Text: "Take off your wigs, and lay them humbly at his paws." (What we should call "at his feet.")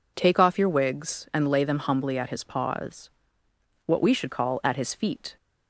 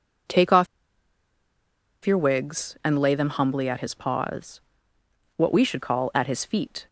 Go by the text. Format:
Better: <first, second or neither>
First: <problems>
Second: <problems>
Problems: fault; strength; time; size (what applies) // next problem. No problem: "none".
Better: first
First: none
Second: pauses between "off" and "your"; strong; at 0.6 s; 1.3 s long